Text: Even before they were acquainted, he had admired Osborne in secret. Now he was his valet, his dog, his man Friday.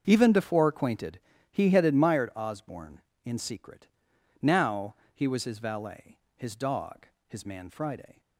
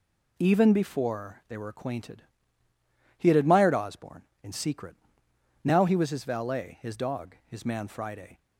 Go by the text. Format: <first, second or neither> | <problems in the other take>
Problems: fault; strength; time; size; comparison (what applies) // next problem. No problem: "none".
second | starts louder than the rest; until 1.0 s; 6.5 dB // skips "they were"; at 0.6 s // pauses between "Now" and "he"; slight; at 4.9 s; 0.20 s long